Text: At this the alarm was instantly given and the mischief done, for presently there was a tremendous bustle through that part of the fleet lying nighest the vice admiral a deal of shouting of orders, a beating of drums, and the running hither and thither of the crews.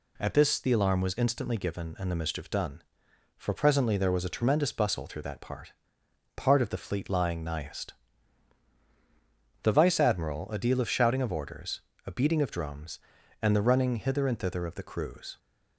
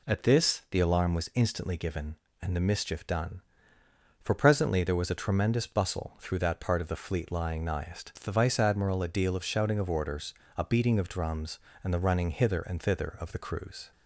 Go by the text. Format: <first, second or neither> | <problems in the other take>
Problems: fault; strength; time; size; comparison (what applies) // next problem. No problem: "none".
second | says "part" twice; at 6.3 s // pauses between "nighest" and "the"; strong; at 7.9 s; 1.6 s long